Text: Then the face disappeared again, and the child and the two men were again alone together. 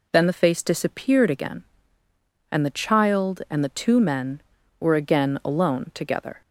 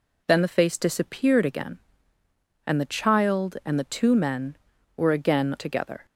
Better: first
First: none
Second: skips "alone"; at 5.5 s

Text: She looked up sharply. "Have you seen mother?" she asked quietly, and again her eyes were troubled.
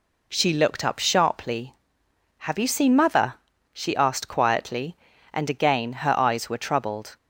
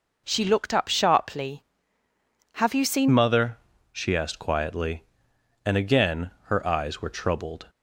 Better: first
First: none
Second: changes voice at "mother"; from 3.0 s on; 4.6 s long // pauses between "again" and "her"; slight; at 6.3 s; 0.16 s long

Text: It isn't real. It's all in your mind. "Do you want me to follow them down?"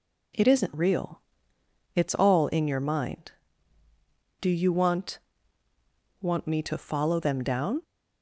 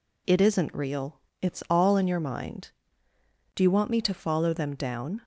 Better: second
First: says "want" twice; at 6.2 s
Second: none

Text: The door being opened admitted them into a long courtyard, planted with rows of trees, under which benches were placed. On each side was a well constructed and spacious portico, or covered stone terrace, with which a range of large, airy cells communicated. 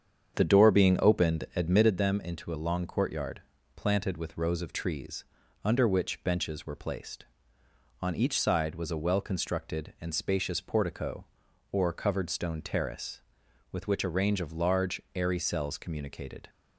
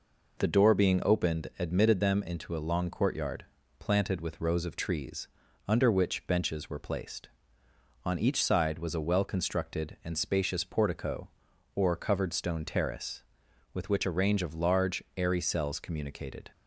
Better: second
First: starts louder than the rest; strong; until 1.9 s; 7.5 dB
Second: none

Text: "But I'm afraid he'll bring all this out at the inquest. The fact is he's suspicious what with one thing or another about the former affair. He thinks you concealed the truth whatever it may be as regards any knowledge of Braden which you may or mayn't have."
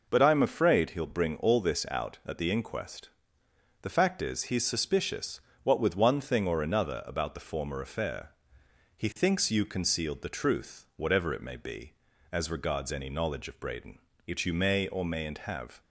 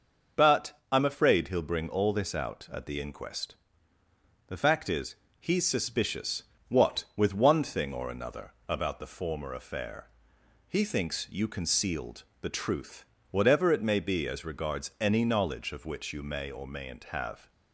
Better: first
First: pauses between "suspicious" and "what"; slight; at 5.3 s; 0.24 s long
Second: starts louder than the rest; noticeable; until 1.4 s; 6 dB // pauses between "is" and "he's"; slight; at 5.1 s; 0.24 s long // pauses between "suspicious" and "what"; slight; at 6.4 s; 0.26 s long // pauses between "another" and "about"; slight; at 8.5 s; 0.15 s long // pauses between "concealed" and "the"; slight; at 12.2 s; 0.18 s long // pauses between "truth" and "whatever"; slight; at 13.0 s; 0.28 s long // skips "Braden"; at 15.8 s

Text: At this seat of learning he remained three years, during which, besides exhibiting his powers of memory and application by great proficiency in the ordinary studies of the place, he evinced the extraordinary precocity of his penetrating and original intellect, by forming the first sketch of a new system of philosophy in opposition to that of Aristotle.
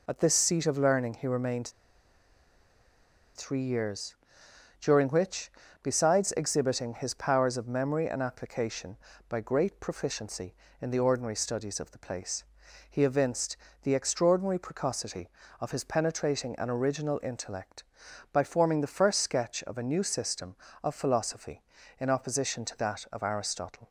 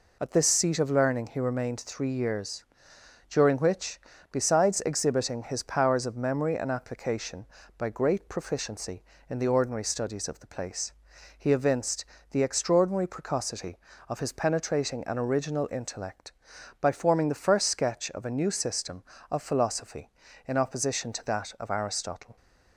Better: second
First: pauses between "remained" and "three"; strong; at 1.6 s; 1.6 s long // pauses between "evinced" and "the"; slight; at 13.5 s; 0.26 s long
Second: pauses between "evinced" and "the"; slight; at 12.0 s; 0.26 s long

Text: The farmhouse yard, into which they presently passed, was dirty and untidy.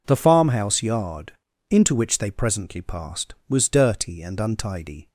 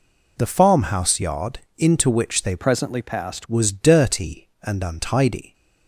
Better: first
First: none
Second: changes voice from "presently" to "passed"; from 2.5 to 3.4 s; 0.9 s long

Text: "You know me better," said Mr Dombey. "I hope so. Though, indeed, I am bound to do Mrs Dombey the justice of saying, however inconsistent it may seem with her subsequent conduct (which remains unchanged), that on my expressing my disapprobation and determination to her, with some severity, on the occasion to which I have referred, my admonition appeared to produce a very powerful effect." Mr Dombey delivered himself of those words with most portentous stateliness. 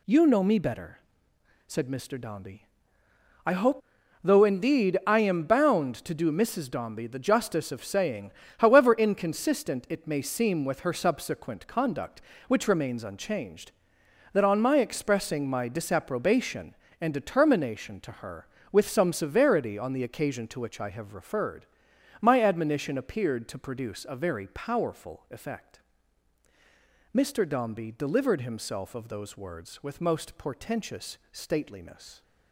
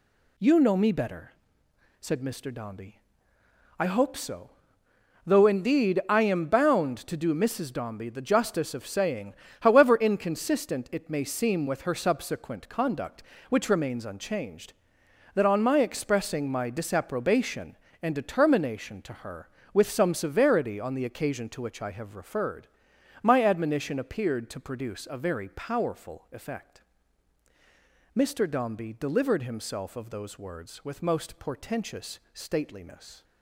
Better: second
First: skips "so"; at 4.0 s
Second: none

